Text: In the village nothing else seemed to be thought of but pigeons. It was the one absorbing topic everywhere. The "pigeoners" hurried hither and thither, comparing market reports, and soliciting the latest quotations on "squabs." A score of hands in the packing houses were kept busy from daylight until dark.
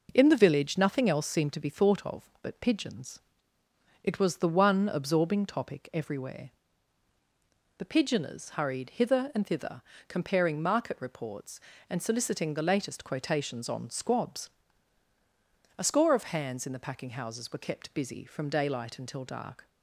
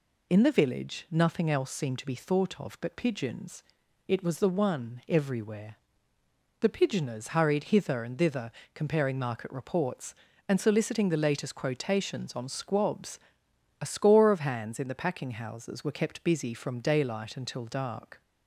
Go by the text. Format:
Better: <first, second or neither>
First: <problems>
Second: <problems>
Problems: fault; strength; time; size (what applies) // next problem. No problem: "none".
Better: first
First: none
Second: skips "absorbing topic"; at 5.0 s